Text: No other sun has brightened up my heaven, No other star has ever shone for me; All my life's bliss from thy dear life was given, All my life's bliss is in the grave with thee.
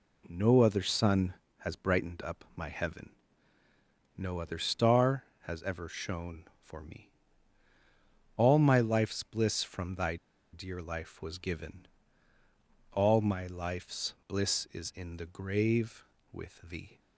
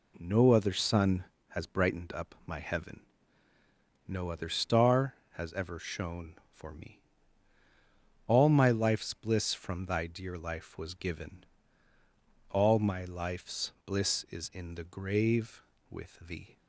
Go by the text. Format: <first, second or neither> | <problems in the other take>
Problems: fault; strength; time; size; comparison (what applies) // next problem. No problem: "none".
second | pauses between "thy" and "dear"; at 10.1 s; 0.36 s long